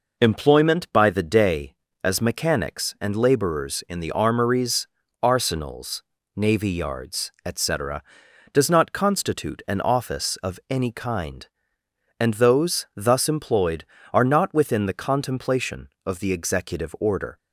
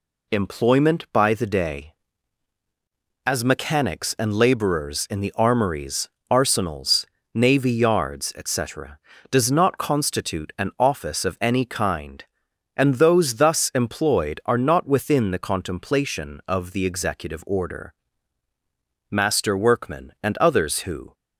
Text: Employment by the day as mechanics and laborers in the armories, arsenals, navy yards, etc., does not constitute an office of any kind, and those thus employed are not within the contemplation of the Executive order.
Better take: first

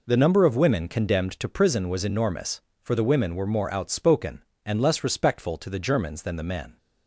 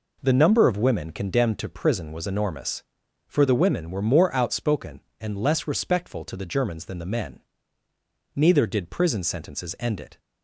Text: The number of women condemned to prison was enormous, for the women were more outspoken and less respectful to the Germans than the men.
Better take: first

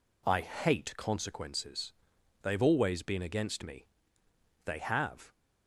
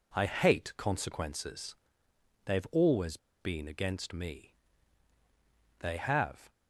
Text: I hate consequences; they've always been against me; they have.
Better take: first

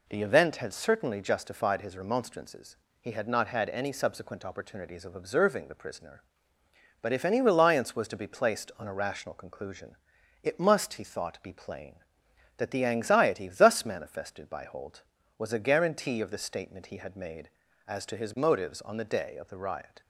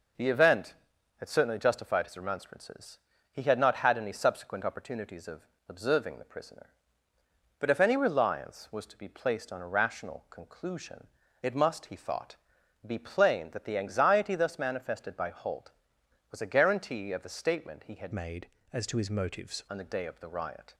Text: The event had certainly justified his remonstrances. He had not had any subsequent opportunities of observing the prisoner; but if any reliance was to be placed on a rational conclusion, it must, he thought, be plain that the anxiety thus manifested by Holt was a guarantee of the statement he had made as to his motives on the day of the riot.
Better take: first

